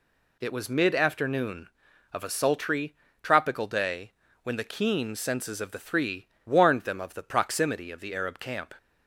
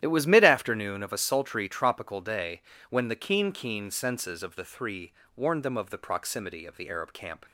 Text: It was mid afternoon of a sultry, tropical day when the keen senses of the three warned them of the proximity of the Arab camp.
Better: first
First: pauses between "day" and "when"; slight; at 4.1 s; 0.30 s long // pauses between "three" and "warned"; slight; at 6.2 s; 0.18 s long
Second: starts louder than the rest; strong; until 1.0 s; 11 dB // pauses between "day" and "when"; slight; at 2.6 s; 0.26 s long // says "keen" twice; at 3.5 s // pauses between "three" and "warned"; slight; at 5.1 s; 0.24 s long

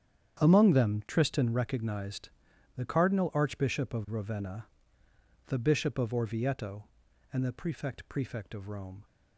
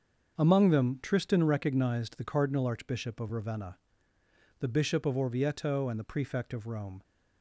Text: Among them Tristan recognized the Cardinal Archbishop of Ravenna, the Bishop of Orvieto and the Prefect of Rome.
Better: second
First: starts louder than the rest; strong; until 1.4 s; 8.5 dB // pauses between "recognized" and "the"; noticeable; at 2.2 s; 0.48 s long // says "Prefect" twice; at 8.0 s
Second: starts louder than the rest; until 1.4 s; 6.5 dB

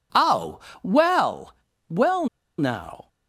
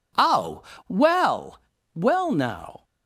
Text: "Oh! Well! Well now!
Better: second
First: pauses between "Well" and "now"; slight; at 2.2 s; 0.32 s long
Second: none

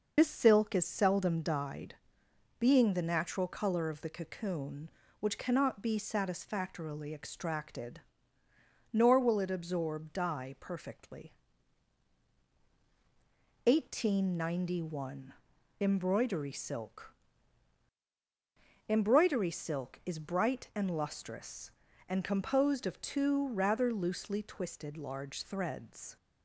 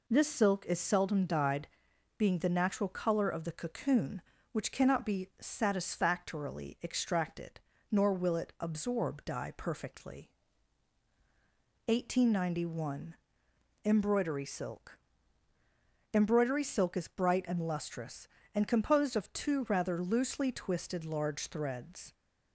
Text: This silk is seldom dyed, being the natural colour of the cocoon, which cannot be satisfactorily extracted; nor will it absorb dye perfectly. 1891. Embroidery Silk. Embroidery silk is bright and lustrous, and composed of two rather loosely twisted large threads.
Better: second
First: loses the start of "This"; at 0.1 s; 40 ms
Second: none

